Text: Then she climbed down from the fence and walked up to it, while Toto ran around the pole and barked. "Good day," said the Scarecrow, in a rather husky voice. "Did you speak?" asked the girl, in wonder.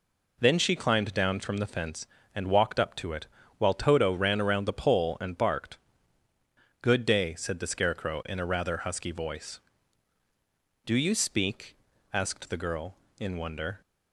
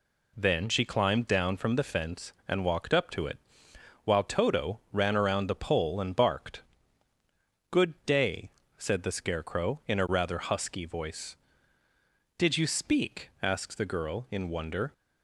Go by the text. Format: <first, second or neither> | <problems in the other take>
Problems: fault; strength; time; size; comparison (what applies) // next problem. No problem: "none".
second | says "Do" for "Did"; at 10.8 s